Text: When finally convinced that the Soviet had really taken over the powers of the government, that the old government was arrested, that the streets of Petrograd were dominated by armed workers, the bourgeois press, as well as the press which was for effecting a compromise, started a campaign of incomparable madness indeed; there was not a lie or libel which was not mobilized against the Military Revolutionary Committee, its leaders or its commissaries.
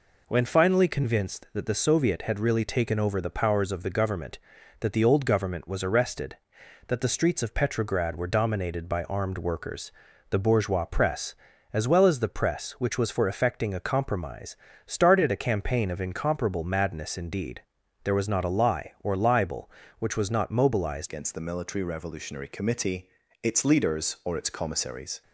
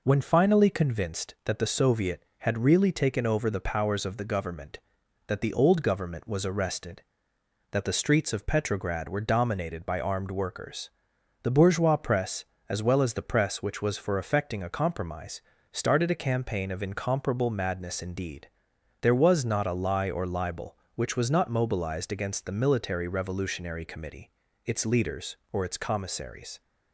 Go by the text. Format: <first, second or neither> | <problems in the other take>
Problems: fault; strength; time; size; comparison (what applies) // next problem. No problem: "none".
second | changes voice at "against"; from 21.0 s on; 4.2 s long